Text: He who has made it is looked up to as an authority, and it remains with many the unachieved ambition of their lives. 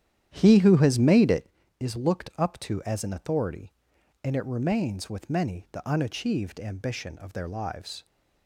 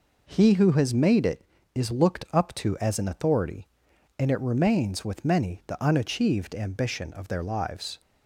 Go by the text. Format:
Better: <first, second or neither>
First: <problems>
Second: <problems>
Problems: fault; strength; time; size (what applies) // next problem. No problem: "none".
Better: second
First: starts louder than the rest; strong; until 1.5 s; 10.5 dB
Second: none